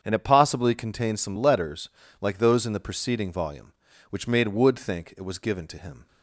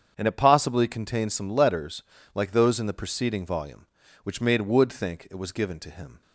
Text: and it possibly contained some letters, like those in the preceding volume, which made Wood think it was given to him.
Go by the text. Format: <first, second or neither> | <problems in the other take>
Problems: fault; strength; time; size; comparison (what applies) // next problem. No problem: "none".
neither | starts louder than the rest; strong; the same in both